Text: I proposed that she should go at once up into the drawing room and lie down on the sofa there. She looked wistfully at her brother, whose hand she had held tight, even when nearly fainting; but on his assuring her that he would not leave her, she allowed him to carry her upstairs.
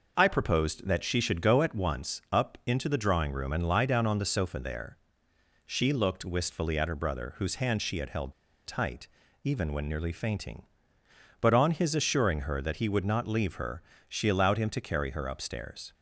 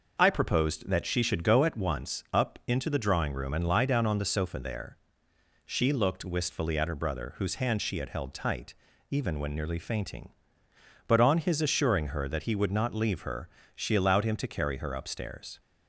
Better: second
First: pauses between "held" and "tight"; slight; at 8.3 s; 0.34 s long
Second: none

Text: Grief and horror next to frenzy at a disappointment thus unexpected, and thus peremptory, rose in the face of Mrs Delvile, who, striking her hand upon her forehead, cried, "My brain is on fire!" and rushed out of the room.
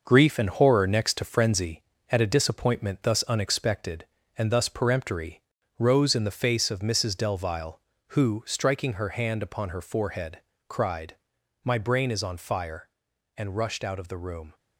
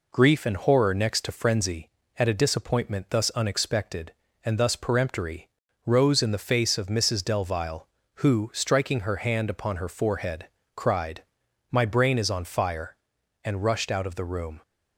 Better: second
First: gets quieter; throughout; 6.5 dB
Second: none

